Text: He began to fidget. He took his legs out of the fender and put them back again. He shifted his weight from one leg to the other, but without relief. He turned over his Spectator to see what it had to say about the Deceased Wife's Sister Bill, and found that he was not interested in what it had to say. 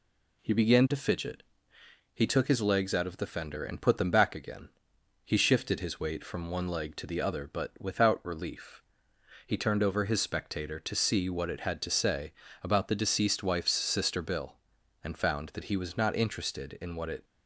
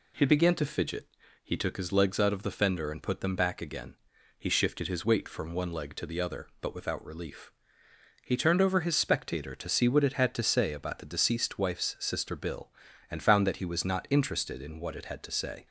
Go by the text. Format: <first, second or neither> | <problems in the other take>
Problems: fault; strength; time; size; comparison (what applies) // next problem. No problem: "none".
second | pauses between "say" and "about"; slight; at 12.3 s; 0.30 s long // stops before "had to say"; at 17.2 s